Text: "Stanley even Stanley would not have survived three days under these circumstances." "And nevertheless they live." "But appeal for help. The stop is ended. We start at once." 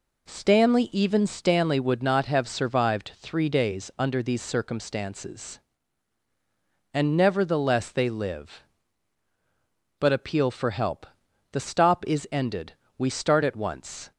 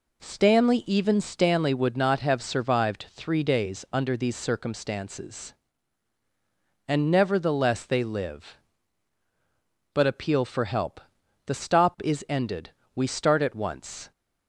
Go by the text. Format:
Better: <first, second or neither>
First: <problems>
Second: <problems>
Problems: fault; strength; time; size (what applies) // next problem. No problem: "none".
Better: neither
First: none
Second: none